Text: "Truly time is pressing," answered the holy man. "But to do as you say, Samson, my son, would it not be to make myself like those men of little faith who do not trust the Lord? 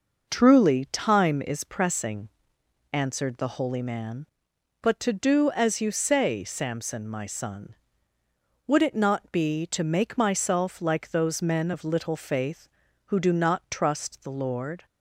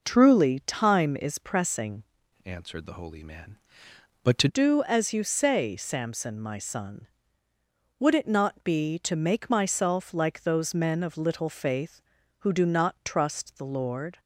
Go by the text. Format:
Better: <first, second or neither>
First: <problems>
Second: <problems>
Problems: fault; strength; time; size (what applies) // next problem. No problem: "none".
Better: first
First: none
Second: changes voice from "answered" to "to"; from 2.4 to 4.4 s; 2.0 s long